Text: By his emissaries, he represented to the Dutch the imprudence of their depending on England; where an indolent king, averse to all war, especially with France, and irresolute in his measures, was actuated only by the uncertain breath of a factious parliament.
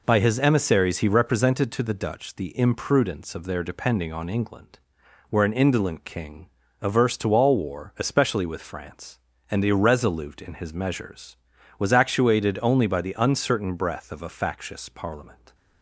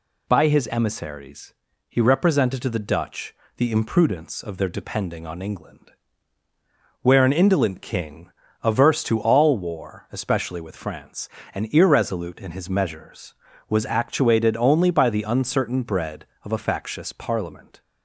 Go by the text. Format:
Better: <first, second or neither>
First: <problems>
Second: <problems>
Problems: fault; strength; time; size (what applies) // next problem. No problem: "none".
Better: first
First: none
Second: pauses between "Dutch" and "the"; slight; at 3.3 s; 0.22 s long // says "bread" for "breath"; at 15.8 s